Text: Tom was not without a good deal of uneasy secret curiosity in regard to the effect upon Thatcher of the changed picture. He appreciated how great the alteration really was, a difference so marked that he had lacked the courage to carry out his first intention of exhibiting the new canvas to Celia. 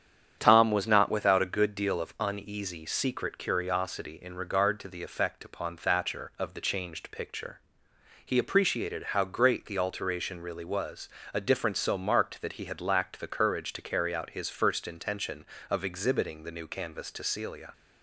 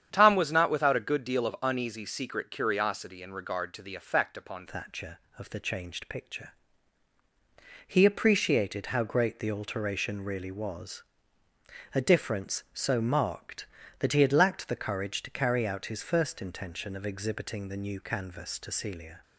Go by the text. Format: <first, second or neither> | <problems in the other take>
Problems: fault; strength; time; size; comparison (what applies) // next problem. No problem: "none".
first | starts louder than the rest; strong; until 1.1 s; 9 dB; strong in the first // changes voice at "Thatcher"; from 4.6 s on; 14.6 s long